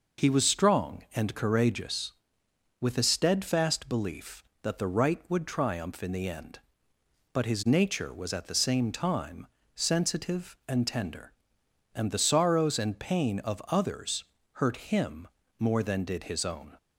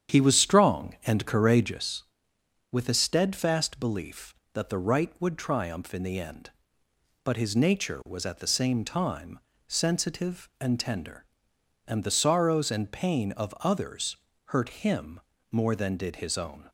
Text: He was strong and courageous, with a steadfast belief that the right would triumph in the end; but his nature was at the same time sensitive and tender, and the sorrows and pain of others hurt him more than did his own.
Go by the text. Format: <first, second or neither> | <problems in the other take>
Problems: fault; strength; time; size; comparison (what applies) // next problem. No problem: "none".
first | starts louder than the rest; strong; until 1.9 s; 8.5 dB // pauses between "time" and "sensitive"; slight; at 9.3 s; 0.26 s long; slight in the first // pauses between "others" and "hurt"; slight; at 14.1 s; 0.34 s long; slight in the first // pauses between "him" and "more"; slight; at 15.1 s; 0.30 s long; slight in the first